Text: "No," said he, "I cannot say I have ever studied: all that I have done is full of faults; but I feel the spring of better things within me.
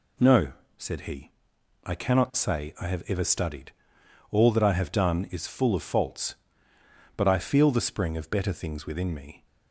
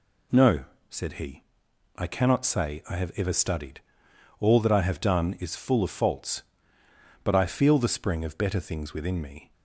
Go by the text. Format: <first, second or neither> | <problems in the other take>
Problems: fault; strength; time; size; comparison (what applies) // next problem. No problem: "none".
neither | none